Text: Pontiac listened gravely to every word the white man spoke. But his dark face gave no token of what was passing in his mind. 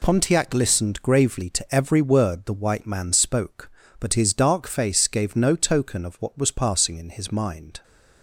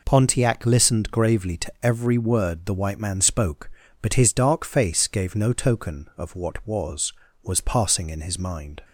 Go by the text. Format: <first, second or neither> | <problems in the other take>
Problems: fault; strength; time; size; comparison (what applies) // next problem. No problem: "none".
first | says "was" twice; at 7.4 s